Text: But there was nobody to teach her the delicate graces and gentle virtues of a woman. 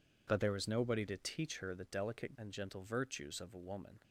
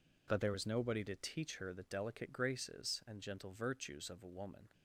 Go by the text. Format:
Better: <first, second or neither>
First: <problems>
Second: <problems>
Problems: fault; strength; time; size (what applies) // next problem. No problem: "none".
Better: second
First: skips "graces"; at 2.3 s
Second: none